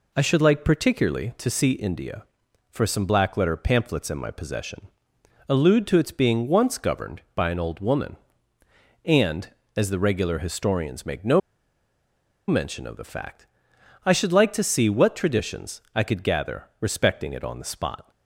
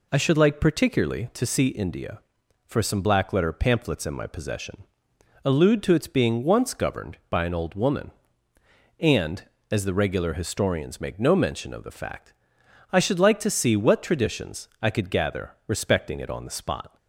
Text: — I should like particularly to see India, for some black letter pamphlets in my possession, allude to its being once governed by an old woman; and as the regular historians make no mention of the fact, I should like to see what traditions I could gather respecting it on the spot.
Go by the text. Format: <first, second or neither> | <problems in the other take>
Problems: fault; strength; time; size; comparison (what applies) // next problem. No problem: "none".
second | pauses between "no" and "mention"; at 11.4 s; 1.0 s long